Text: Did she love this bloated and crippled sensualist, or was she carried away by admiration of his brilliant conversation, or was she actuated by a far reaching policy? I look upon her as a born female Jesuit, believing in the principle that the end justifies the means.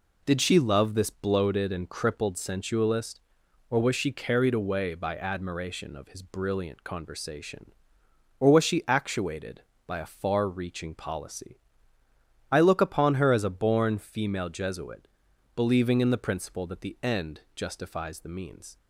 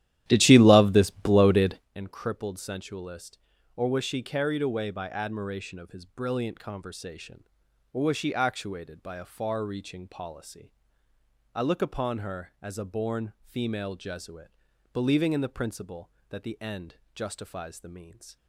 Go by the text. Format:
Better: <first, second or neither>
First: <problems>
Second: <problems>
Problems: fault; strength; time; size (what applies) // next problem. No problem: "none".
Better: first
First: pauses between "end" and "justifies"; slight; at 17.4 s; 0.16 s long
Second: starts louder than the rest; strong; until 1.9 s; 12.5 dB // pauses between "end" and "justifies"; slight; at 16.9 s; 0.18 s long